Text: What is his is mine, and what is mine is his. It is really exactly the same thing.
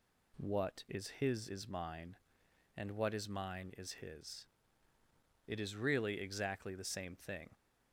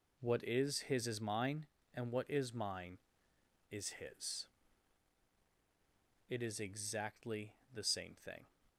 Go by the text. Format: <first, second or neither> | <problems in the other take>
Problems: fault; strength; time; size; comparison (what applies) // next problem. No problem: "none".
first | skips "really"; at 6.5 s // pauses between "exactly" and "the"; slight; at 7.5 s; 0.20 s long